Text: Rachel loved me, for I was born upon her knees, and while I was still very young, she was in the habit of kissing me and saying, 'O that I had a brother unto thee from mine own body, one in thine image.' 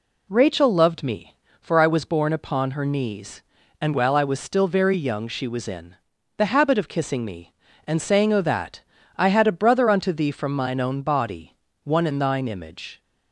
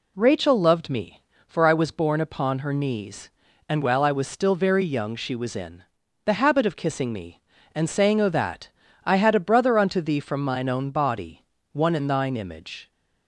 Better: neither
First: pauses between "in" and "the"; at 5.9 s; 0.42 s long // pauses between "that" and "I"; at 8.7 s; 0.38 s long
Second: pauses between "in" and "the"; at 5.8 s; 0.42 s long // pauses between "that" and "I"; at 8.6 s; 0.38 s long

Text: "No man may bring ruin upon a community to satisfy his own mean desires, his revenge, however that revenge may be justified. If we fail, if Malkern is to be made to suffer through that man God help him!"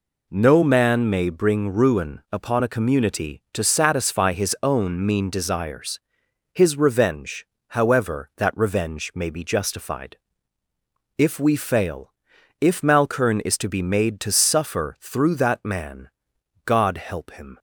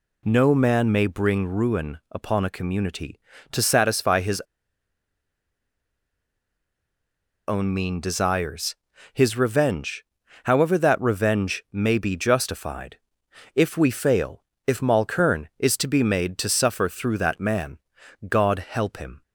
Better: first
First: pauses between "man" and "God"; noticeable; at 16.0 s; 0.56 s long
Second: pauses between "his" and "own"; strong; at 4.4 s; 3.0 s long // pauses between "man" and "God"; noticeable; at 17.7 s; 0.48 s long

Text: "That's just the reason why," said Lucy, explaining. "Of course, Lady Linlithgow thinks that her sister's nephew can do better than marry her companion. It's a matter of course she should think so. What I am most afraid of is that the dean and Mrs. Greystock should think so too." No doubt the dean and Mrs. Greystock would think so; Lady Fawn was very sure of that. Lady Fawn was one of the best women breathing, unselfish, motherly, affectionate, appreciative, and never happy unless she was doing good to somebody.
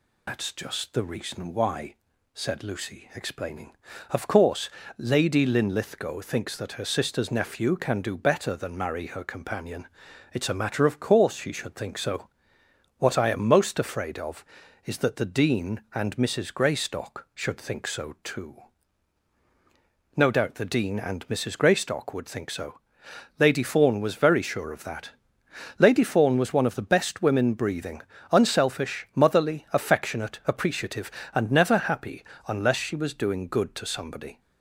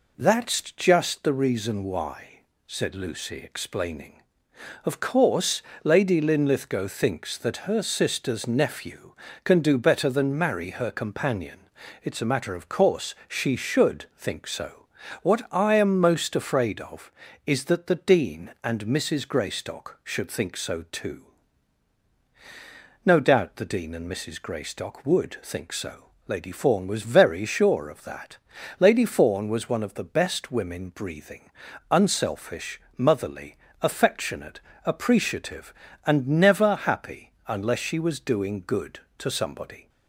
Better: second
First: loses the start of "That's"; at 0.2 s; 85 ms // pauses between "happy" and "unless"; slight; at 32.2 s; 0.24 s long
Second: pauses between "happy" and "unless"; slight; at 37.3 s; 0.16 s long

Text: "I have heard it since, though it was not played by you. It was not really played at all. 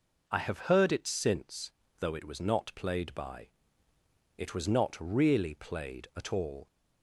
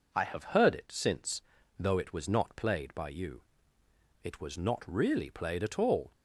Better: second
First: skips "you"; at 3.9 s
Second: none

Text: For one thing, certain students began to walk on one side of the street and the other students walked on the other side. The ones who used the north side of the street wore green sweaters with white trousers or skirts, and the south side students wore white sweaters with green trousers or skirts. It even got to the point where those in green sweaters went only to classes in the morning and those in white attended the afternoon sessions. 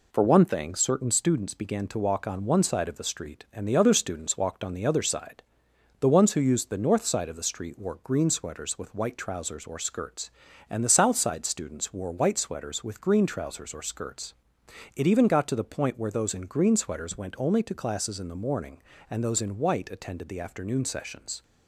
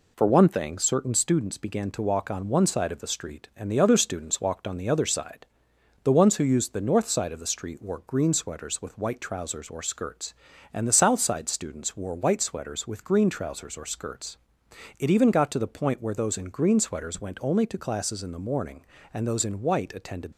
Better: first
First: none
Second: stops before "the afternoon sessions"; at 20.3 s

